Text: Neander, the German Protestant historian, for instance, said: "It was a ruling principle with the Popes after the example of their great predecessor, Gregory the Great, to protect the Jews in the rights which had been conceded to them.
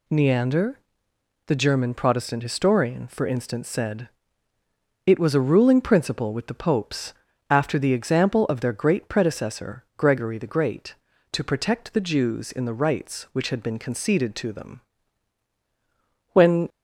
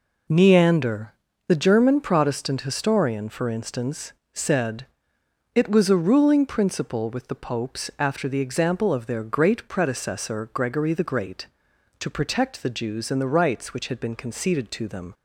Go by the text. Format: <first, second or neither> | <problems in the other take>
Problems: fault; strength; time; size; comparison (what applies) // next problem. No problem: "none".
second | pauses between "Popes" and "after"; at 7.1 s; 0.38 s long // goes on to say "When"; slight; from 16.3 s on; 0.36 s long